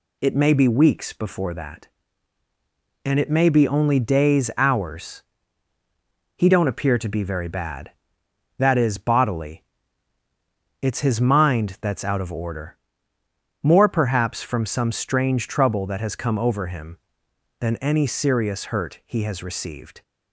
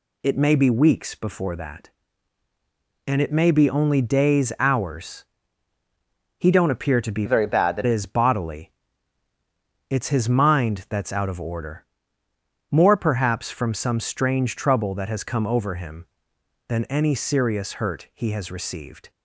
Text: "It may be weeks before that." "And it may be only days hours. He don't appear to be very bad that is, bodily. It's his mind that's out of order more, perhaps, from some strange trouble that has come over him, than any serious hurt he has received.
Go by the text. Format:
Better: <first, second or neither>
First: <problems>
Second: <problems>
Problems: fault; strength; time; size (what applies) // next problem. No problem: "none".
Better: first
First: pauses between "order" and "more"; noticeable; at 12.7 s; 0.84 s long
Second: changes voice from "very" to "that"; from 7.2 to 7.8 s; 0.6 s long // pauses between "order" and "more"; noticeable; at 11.8 s; 0.84 s long